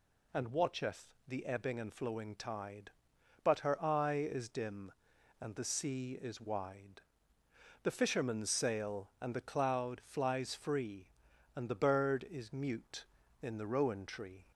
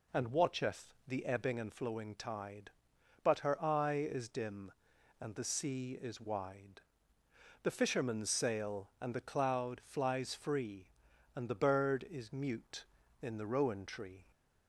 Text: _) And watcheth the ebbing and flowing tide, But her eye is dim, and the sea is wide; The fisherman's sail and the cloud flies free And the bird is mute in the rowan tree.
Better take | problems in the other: first | starts louder than the rest; slight; until 1.8 s; 2.5 dB

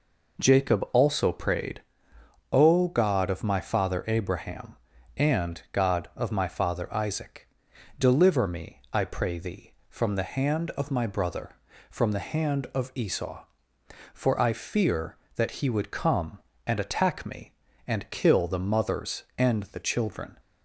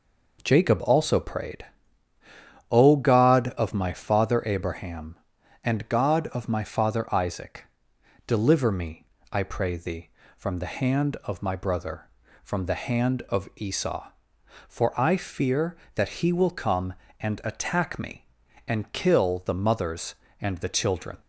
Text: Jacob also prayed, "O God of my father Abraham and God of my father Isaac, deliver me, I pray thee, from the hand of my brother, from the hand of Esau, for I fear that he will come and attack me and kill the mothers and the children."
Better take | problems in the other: second | says "would" for "will"; at 15.6 s

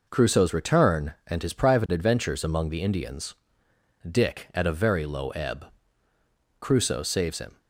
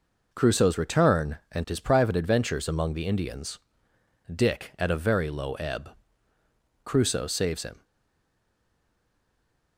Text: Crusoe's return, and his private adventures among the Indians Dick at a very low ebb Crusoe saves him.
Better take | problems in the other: first | pauses between "Indians" and "Dick"; noticeable; at 3.5 s; 0.74 s long; noticeable in the first // pauses between "ebb" and "Crusoe"; noticeable; at 5.8 s; 0.94 s long; noticeable in the first // stays silent after the last word; noticeable; from 7.8 s on; 1.9 s long

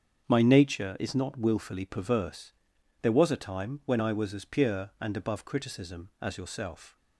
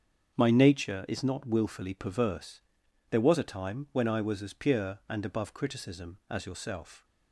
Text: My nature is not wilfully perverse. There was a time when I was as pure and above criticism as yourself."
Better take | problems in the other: neither | starts louder than the rest; strong; the same in both

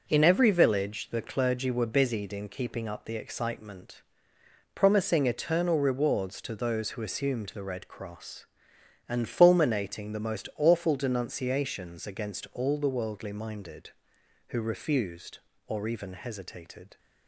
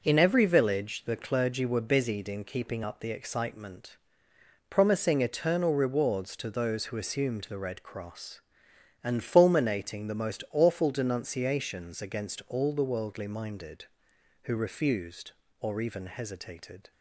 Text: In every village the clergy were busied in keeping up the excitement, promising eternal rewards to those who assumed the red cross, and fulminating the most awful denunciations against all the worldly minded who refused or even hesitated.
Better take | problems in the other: neither | none

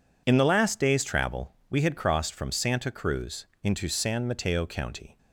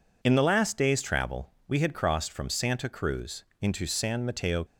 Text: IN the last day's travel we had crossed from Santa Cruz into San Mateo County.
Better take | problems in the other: first | pauses between "travel" and "we"; slight; at 1.4 s; 0.16 s long; slight in the first // pauses between "Cruz" and "into"; slight; at 3.4 s; 0.16 s long; slight in the first // stops before "County"; at 4.6 s

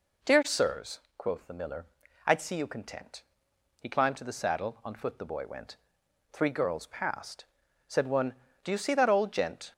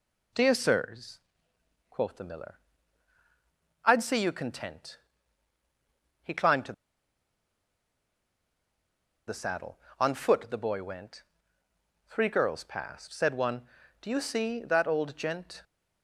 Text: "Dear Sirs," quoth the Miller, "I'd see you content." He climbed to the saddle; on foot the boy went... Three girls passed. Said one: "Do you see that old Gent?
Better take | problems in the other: first | pauses between "to" and "the"; strong; at 6.7 s; 2.5 s long

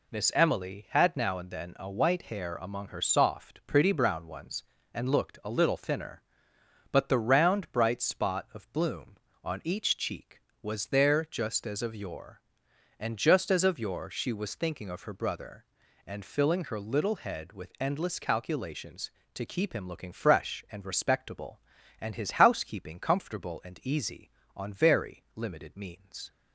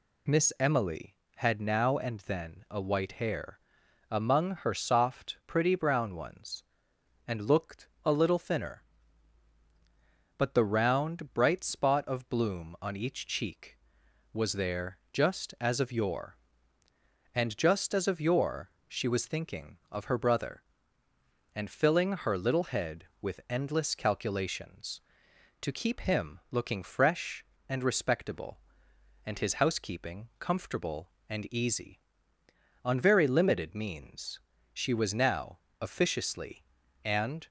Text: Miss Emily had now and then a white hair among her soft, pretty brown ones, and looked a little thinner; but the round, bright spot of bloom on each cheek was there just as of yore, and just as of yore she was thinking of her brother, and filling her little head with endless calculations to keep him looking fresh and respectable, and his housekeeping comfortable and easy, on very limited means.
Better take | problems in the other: first | pauses between "hair" and "among"; noticeable; at 3.5 s; 0.52 s long // pauses between "looked" and "a"; slight; at 7.8 s; 0.16 s long // pauses between "there" and "just"; slight; at 14.9 s; 0.16 s long // pauses between "yore" and "she"; slight; at 18.6 s; 0.20 s long // goes on to say "She was now officiously and"; strong; from 34.7 s on; 2.7 s long

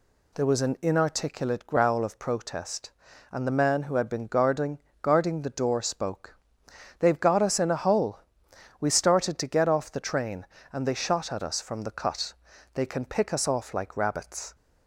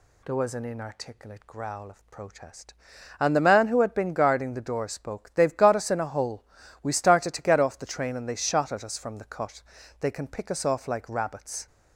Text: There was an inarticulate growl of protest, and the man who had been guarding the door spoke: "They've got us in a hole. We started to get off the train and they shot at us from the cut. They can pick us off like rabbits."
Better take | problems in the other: second | says "guarding" twice; at 5.0 s

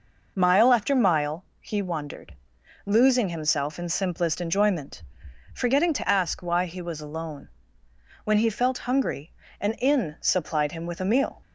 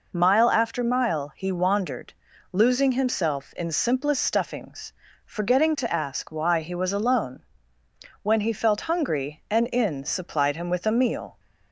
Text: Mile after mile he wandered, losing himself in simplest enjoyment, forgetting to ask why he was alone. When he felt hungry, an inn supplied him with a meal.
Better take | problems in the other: first | says "stuffings" for "enjoyment"; at 4.2 s

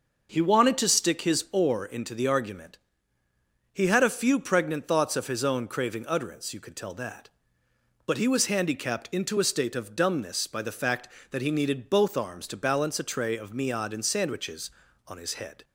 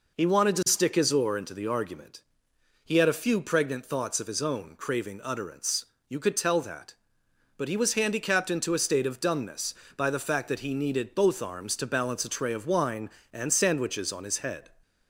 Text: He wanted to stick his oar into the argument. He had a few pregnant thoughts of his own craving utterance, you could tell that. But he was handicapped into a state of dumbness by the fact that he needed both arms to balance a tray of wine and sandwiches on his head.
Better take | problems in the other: second | says "miad" for "wine"; at 13.5 s

